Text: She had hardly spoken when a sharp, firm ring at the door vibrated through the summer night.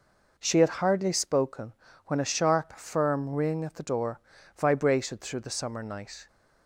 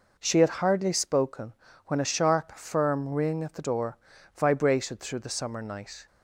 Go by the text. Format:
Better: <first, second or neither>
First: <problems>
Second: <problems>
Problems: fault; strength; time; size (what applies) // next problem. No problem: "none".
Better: neither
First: pauses between "spoken" and "when"; slight; at 1.7 s; 0.34 s long // pauses between "door" and "vibrated"; at 4.1 s; 0.36 s long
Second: pauses between "spoken" and "when"; slight; at 1.5 s; 0.34 s long // pauses between "door" and "vibrated"; at 3.9 s; 0.38 s long